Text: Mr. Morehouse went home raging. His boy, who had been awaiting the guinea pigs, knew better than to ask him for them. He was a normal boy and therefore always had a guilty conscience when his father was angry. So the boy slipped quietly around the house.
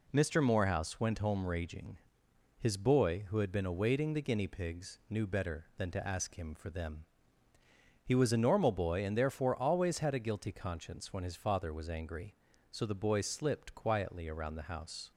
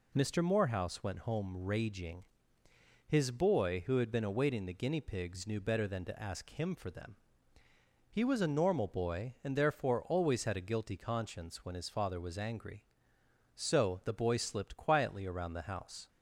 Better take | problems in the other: neither | none

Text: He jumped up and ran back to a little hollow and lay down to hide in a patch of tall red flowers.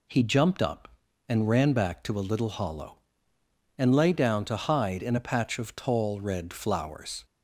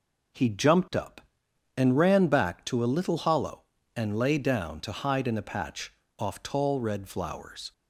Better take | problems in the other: first | says "off" for "of"; at 6.1 s

